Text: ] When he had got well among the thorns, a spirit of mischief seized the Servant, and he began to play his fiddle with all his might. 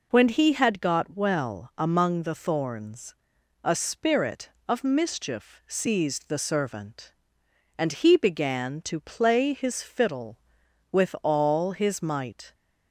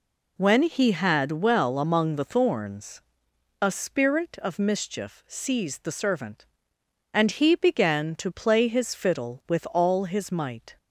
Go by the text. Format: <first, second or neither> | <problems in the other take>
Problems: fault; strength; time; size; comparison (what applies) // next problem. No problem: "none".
first | skips "got"; at 1.3 s